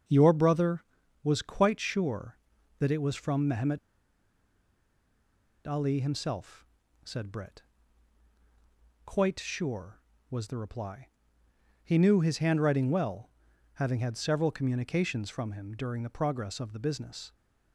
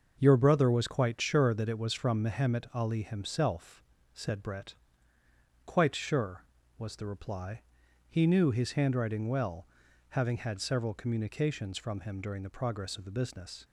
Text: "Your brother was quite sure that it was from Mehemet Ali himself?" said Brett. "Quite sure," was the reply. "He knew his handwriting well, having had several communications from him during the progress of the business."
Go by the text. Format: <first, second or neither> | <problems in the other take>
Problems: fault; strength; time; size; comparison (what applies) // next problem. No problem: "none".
second | starts louder than the rest; until 1.4 s; 7 dB; also in the second // pauses between "Mehemet" and "Ali"; strong; at 3.7 s; 1.8 s long